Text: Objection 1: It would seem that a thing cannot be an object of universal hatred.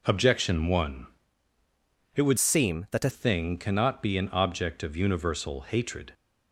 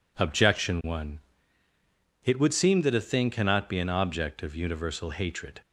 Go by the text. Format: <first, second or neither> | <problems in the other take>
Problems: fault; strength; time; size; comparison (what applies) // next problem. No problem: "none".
second | changes voice from "seem" to "a"; from 2.3 to 3.0 s; 0.7 s long